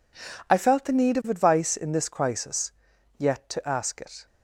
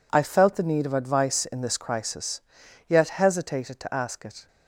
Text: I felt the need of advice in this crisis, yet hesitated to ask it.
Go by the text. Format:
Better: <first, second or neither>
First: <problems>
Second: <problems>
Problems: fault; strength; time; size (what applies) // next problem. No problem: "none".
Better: second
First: skips "hesitated"; at 3.4 s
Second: none